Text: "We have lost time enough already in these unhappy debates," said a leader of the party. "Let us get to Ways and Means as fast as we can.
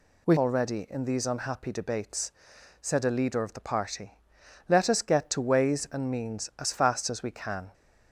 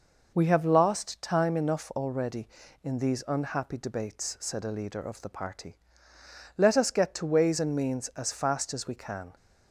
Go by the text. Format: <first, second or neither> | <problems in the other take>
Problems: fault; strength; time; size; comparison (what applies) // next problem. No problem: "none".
second | skips "have lost time enough"; at 0.3 s